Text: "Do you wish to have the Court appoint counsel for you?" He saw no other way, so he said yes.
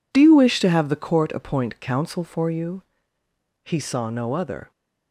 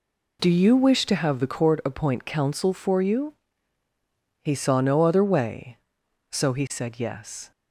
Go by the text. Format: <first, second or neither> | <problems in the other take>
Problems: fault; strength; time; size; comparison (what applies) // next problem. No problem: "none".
second | stops before "way so he said yes"; at 4.7 s